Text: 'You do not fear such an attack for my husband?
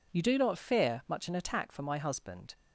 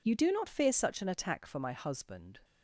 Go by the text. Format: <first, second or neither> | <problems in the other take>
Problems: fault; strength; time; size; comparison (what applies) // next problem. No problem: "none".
second | says "much" for "such"; at 1.0 s